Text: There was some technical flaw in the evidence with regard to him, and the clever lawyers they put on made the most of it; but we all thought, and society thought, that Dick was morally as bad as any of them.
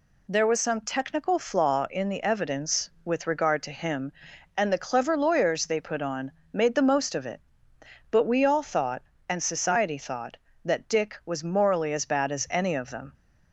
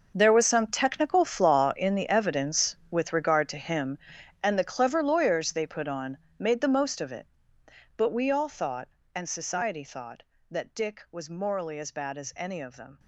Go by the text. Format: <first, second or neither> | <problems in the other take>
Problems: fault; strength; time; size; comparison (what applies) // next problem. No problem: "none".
first | gets quieter; strong; throughout; 14.5 dB // pauses between "on" and "made"; slight; at 6.1 s; 0.18 s long; slight in the first